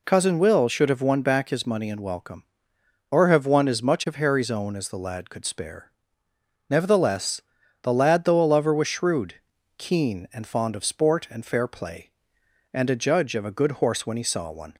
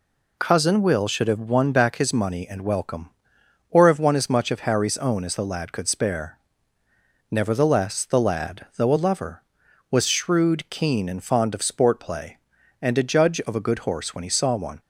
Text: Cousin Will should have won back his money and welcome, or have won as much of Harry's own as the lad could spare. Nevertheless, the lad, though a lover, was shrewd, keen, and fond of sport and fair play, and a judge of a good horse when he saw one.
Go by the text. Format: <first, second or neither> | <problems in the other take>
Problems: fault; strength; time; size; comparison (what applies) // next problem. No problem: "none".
first | skips "and fair"; at 11.9 s